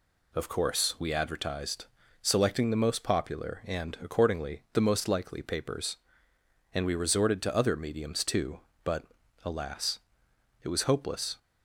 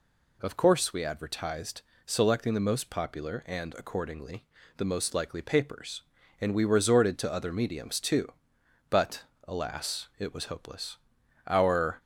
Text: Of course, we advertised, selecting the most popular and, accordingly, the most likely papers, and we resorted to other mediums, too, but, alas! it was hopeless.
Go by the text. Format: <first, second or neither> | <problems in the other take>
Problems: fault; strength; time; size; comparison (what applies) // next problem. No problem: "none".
first | goes on to say "Our"; from 11.4 s on; 0.54 s long